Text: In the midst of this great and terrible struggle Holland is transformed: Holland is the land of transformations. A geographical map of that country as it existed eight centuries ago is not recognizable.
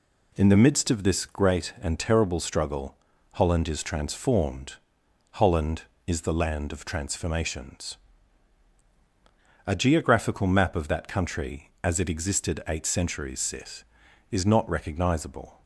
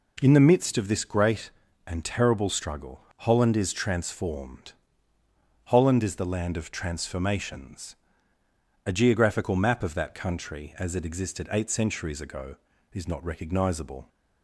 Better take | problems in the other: second | pauses between "struggle" and "Holland"; slight; at 2.9 s; 0.36 s long // says "sith" for "ago"; at 13.4 s

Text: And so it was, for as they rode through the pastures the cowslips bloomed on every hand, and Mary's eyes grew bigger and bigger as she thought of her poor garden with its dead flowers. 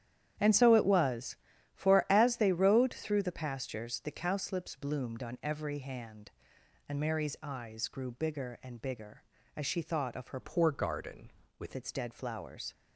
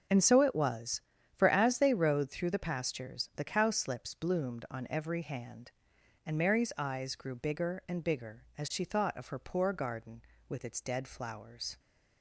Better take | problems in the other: second | starts louder than the rest; strong; until 1.7 s; 10 dB; also in the second // changes voice from "poor" to "with"; from 10.4 to 11.7 s; 1.3 s long

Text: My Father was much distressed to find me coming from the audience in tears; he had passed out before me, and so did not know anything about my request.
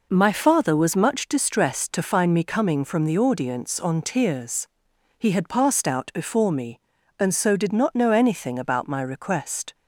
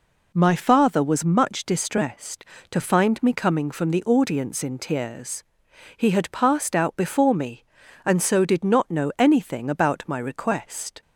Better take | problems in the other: second | says "on" for "in"; at 3.8 s

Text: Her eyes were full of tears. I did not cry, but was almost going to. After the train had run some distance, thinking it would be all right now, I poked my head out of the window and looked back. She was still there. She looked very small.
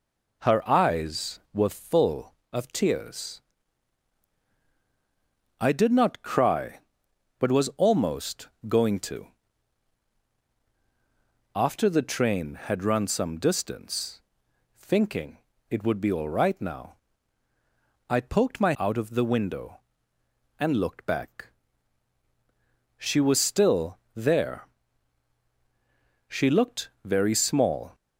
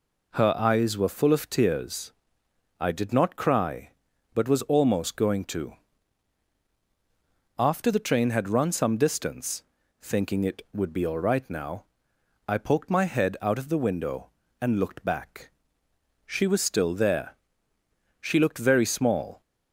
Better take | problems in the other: second | pauses between "almost" and "going"; slight; at 8.4 s; 0.20 s long // pauses between "thinking" and "it"; slight; at 15.3 s; 0.32 s long // skips "head"; at 18.7 s // pauses between "still" and "there"; slight; at 23.9 s; 0.18 s long

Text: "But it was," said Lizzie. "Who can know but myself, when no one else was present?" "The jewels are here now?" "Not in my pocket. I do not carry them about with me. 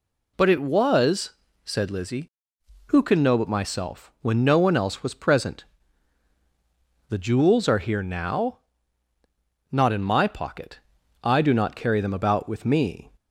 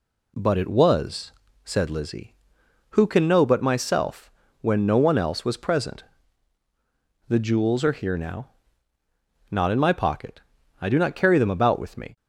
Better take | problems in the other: neither | none

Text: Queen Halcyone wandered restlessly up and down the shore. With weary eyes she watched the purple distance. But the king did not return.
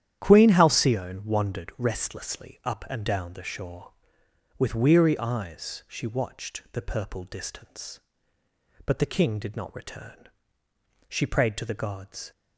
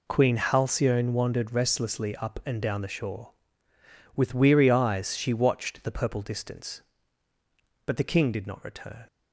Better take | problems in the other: second | starts louder than the rest; strong; until 1.2 s; 10.5 dB // goes on to say "She prayed to the gods"; noticeable; from 11.0 s on; 1.2 s long

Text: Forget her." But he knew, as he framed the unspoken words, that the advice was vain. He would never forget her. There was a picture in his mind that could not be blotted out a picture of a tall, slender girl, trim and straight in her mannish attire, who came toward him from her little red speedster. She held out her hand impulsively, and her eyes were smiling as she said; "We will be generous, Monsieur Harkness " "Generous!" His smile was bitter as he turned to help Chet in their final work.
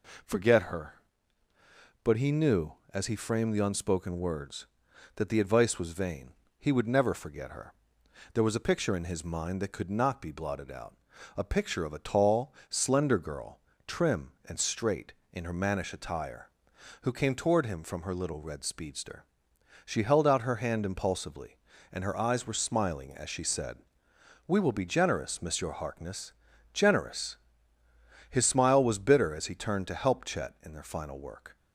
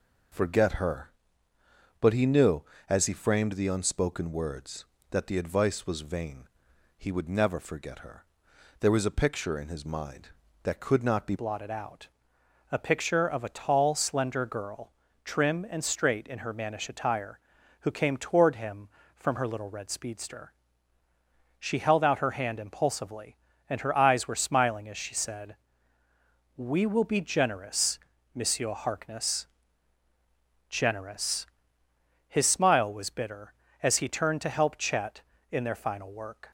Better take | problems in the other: first | changes voice at "blotted"; from 11.3 s on; 25.2 s long // pauses between "out" and "a"; noticeable; at 12.0 s; 0.62 s long; also in the first

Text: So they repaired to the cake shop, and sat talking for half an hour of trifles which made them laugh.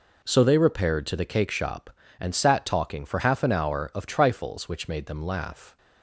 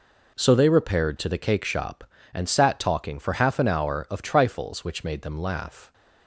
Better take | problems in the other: neither | none

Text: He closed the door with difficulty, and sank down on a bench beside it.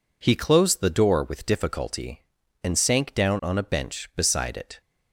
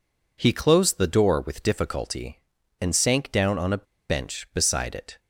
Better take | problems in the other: first | pauses between "a" and "bench"; slight; at 3.8 s; 0.25 s long

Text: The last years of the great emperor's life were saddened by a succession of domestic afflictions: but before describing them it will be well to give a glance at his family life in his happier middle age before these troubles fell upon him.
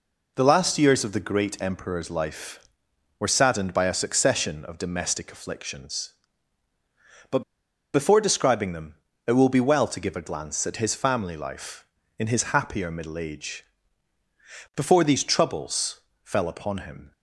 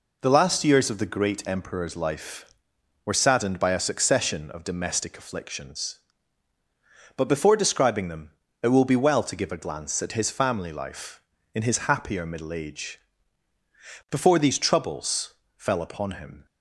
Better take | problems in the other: second | pauses between "but" and "before"; noticeable; at 7.4 s; 0.52 s long // pauses between "them" and "it"; slight; at 8.9 s; 0.32 s long; slight in the second // pauses between "age" and "before"; at 13.6 s; 1.1 s long; also in the second // pauses between "troubles" and "fell"; slight; at 15.9 s; 0.24 s long; slight in the second

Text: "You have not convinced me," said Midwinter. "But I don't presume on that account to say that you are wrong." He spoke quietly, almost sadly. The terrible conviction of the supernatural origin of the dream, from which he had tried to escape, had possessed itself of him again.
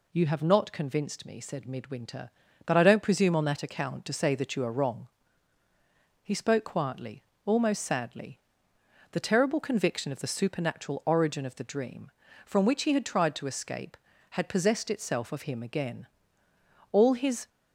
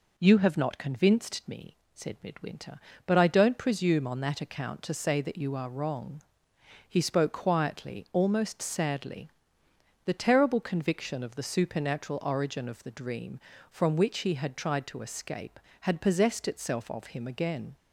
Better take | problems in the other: second | goes on to say "All his"; from 16.9 s on; 0.56 s long

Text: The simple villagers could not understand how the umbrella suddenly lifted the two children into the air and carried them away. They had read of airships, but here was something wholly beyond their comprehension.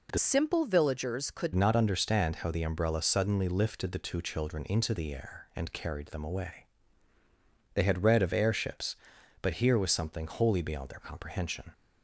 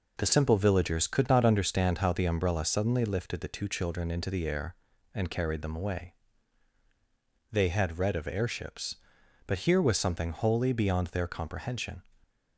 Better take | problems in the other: second | changes voice from "simple" to "could"; from 0.1 to 1.5 s; 1.4 s long

